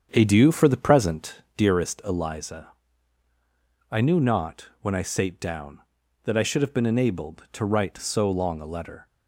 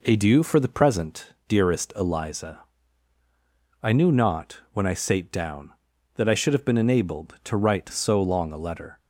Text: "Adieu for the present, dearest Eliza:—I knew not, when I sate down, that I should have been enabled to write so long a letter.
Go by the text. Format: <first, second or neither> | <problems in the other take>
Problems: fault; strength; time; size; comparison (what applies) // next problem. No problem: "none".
second | starts louder than the rest; strong; until 1.9 s; 8 dB